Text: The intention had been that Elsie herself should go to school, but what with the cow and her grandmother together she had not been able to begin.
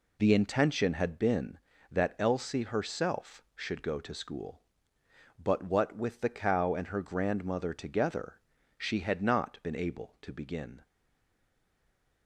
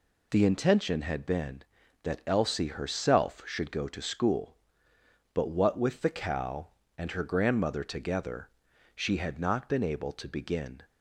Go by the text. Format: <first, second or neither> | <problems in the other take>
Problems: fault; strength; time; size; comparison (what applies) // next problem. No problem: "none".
second | pauses between "together" and "she"; at 8.3 s; 0.40 s long; noticeable in the second // stays silent after the last word; noticeable; from 10.8 s on; 1.4 s long